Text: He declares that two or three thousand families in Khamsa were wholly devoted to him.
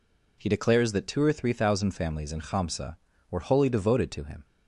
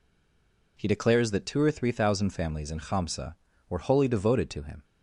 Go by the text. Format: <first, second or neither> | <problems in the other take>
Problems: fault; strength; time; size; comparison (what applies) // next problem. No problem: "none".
first | stays silent before the first word; slight; until 0.7 s; 0.7 s long